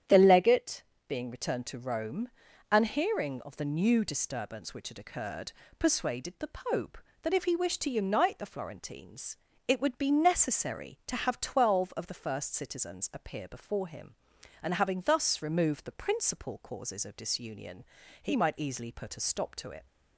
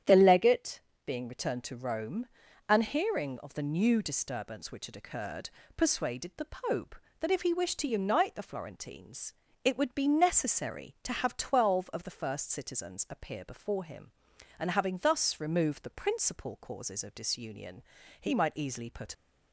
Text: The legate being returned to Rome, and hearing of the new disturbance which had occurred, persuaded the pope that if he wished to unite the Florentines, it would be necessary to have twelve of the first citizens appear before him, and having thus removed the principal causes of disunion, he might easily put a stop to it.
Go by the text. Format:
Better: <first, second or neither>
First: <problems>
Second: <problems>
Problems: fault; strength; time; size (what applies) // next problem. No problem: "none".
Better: first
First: starts louder than the rest; strong; until 1.3 s; 9 dB // pauses between "legate" and "being"; slight; at 0.8 s; 0.24 s long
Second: starts louder than the rest; strong; until 1.2 s; 9 dB // pauses between "legate" and "being"; slight; at 0.8 s; 0.24 s long // stops before "a stop to it"; at 19.1 s